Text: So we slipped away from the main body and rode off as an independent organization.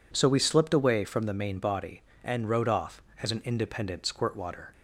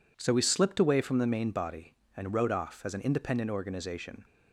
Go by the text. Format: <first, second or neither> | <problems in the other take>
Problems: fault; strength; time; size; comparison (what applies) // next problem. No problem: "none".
second | says "squirtwater" for "organization"; at 4.0 s